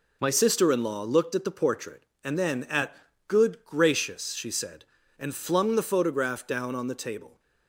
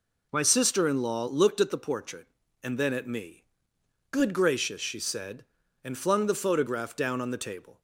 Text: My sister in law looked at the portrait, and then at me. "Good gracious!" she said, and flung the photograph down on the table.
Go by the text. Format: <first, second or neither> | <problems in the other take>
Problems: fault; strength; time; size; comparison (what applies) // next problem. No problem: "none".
second | skips "me"; at 3.1 s